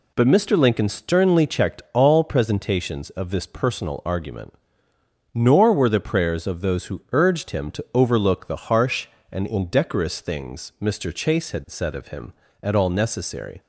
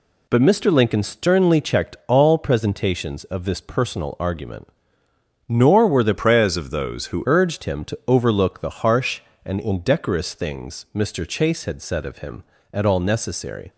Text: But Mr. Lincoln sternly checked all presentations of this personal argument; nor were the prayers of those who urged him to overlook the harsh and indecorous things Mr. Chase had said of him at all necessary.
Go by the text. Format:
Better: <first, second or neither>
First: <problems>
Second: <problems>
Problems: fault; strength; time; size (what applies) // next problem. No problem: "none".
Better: first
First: none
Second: changes voice from "prayers" to "who"; from 6.1 to 7.2 s; 1.1 s long